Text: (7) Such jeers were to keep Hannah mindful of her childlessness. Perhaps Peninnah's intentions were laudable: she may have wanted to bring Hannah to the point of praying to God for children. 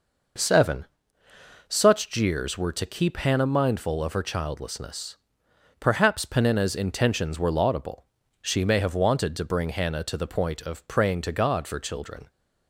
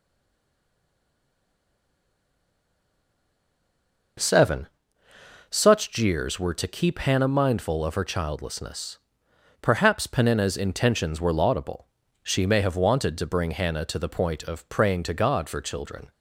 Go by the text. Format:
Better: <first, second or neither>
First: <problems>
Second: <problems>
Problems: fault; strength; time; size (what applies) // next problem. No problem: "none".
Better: first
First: none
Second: stays silent before the first word; strong; until 4.1 s; 4.1 s long